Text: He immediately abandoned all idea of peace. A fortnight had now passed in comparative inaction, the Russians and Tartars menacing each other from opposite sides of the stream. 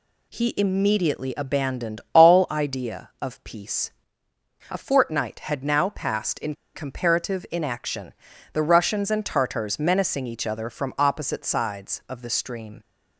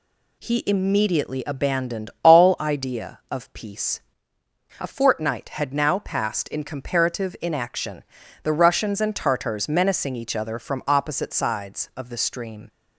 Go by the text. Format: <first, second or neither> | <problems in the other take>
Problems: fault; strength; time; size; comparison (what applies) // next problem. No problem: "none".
second | pauses between "in" and "comparative"; slight; at 6.5 s; 0.20 s long